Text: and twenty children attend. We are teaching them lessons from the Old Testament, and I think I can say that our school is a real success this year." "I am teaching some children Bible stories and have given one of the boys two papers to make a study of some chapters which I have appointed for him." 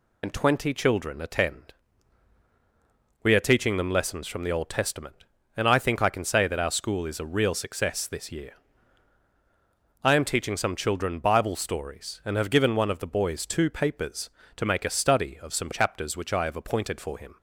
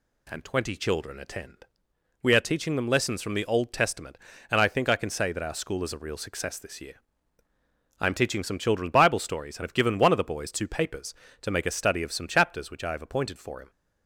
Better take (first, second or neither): second